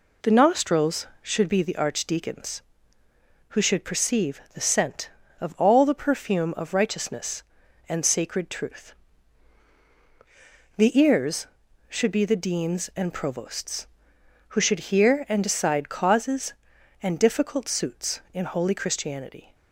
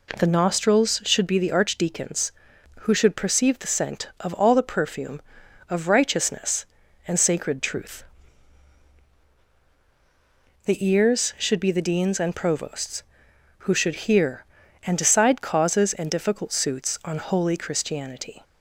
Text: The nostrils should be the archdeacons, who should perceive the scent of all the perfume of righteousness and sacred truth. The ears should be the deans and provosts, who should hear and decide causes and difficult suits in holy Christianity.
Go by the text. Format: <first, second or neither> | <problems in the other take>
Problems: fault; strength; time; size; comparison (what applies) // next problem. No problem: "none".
first | says "on" for "in"; at 17.0 s